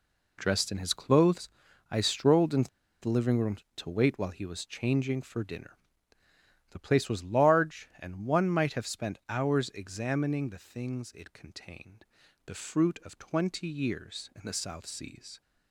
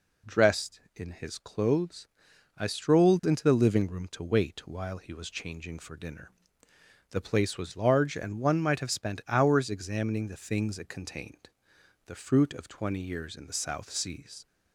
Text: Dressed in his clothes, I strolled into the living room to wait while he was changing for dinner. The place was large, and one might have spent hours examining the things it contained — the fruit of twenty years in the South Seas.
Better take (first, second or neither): second